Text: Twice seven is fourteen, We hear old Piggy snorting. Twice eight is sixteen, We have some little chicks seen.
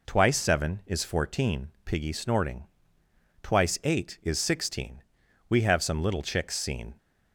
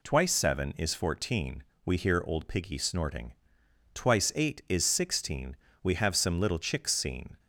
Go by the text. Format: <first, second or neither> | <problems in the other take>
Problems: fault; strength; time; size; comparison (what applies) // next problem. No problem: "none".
second | skips "We hear old"; at 1.7 s